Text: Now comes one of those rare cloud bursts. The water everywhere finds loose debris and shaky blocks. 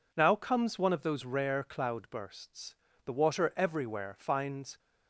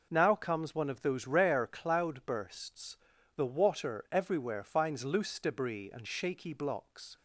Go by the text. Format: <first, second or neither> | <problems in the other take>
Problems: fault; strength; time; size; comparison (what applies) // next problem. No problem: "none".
second | stops before "loose debris and shaky blocks"; at 4.7 s